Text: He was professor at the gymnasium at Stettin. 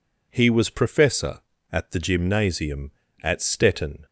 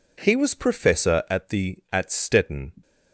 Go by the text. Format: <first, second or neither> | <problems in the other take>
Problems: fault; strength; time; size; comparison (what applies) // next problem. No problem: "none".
first | skips "gymnasium"; at 1.8 s